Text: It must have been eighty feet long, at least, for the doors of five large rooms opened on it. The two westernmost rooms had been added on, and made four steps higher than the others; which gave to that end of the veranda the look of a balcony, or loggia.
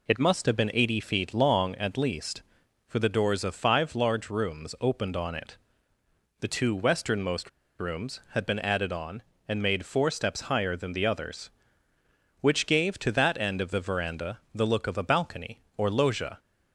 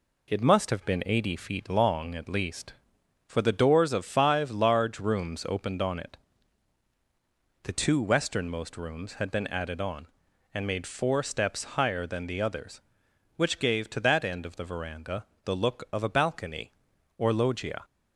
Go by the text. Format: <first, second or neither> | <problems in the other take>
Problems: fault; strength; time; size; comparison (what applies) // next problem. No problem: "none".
second | pauses between "westernmost" and "rooms"; slight; at 7.4 s; 0.29 s long // pauses between "veranda" and "the"; slight; at 14.3 s; 0.16 s long; slight in the second